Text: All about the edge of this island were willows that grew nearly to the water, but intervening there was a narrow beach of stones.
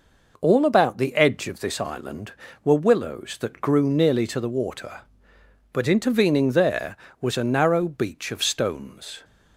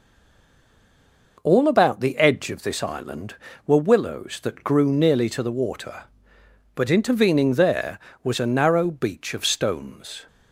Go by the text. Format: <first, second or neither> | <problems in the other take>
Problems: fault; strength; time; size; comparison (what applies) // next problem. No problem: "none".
first | stays silent before the first word; noticeable; until 1.3 s; 1.3 s long